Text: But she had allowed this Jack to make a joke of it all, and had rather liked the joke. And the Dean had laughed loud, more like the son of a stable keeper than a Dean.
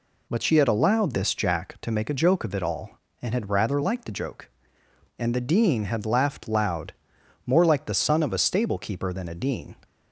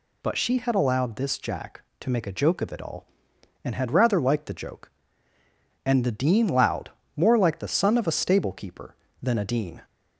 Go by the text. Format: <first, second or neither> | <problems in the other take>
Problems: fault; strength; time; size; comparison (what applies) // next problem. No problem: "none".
first | skips "had laughed"; at 6.4 s